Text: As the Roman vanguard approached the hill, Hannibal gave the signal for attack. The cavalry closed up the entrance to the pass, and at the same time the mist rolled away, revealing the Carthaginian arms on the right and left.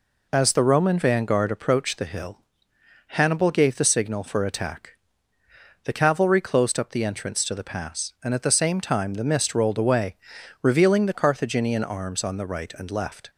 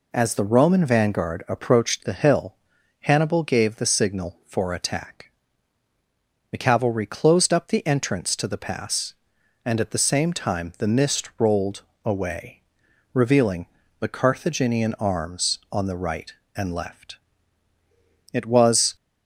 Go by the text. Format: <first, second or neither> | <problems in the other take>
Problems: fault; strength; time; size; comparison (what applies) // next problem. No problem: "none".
first | pauses between "rolled" and "away"; slight; at 11.8 s; 0.20 s long // pauses between "revealing" and "the"; slight; at 13.6 s; 0.32 s long // goes on to say "It was"; noticeable; from 18.3 s on; 0.62 s long